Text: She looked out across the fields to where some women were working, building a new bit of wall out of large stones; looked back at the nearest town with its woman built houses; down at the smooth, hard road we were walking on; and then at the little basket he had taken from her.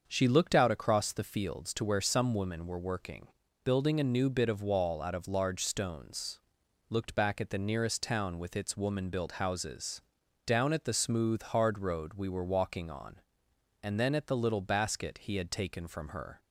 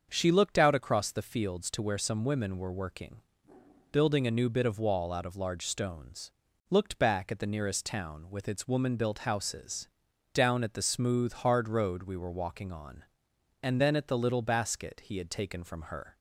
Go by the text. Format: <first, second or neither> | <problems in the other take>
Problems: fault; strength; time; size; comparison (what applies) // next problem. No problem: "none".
neither | starts louder than the rest; the same in both